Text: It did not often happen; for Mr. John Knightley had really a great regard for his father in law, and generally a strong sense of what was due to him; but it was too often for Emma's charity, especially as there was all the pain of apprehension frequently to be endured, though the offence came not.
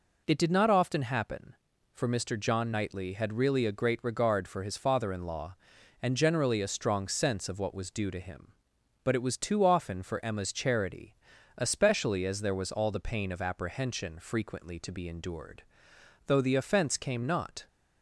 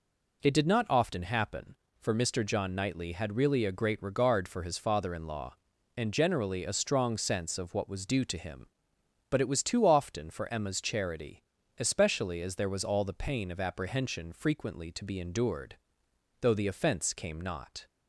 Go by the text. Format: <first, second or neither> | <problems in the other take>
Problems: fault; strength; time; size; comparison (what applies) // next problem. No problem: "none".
neither | none